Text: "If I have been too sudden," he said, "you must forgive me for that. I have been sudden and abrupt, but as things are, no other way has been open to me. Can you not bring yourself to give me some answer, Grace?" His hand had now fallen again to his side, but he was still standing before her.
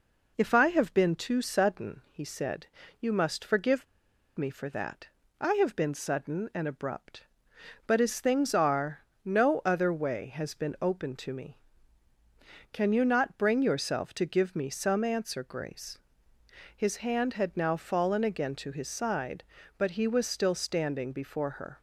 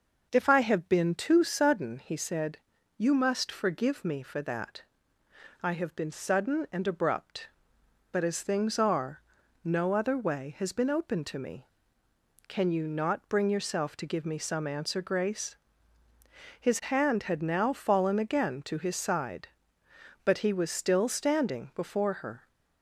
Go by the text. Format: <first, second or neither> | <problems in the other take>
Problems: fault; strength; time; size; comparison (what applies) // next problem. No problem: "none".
second | pauses between "forgive" and "me"; noticeable; at 3.8 s; 0.52 s long